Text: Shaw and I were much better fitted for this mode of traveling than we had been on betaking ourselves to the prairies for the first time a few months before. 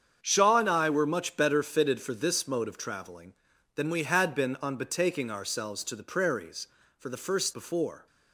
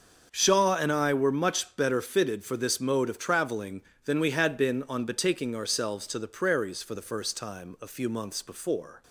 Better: second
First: starts louder than the rest; strong; until 1.2 s; 7.5 dB // skips "time a few months"; at 7.5 s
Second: starts louder than the rest; until 1.3 s; 6.5 dB

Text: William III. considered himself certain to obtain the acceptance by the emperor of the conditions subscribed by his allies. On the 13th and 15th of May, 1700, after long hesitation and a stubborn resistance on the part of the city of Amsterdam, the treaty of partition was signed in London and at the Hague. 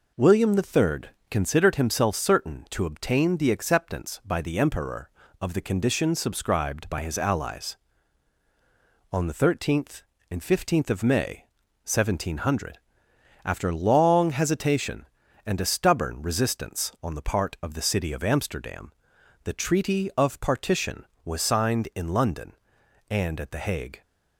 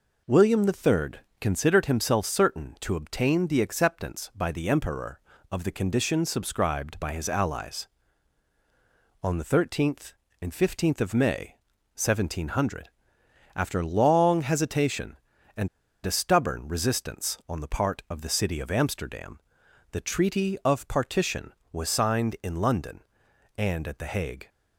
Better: first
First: none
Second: pauses between "and" and "a"; slight; at 15.6 s; 0.36 s long

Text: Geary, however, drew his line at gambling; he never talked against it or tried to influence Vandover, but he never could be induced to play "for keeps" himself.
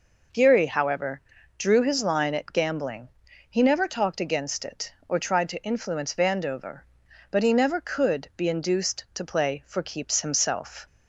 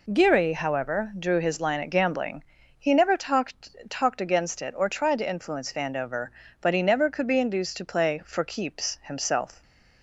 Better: first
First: none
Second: says "talked" twice; at 3.8 s

